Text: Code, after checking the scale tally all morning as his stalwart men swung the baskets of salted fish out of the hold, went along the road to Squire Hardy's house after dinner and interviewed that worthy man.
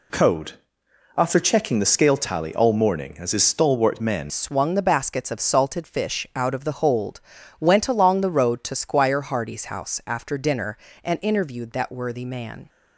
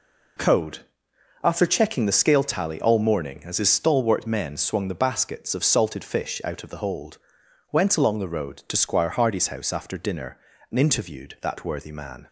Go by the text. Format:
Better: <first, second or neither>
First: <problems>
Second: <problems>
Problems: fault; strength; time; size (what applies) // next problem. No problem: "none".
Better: second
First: changes voice at "swung"; from 4.2 s on; 8.4 s long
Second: none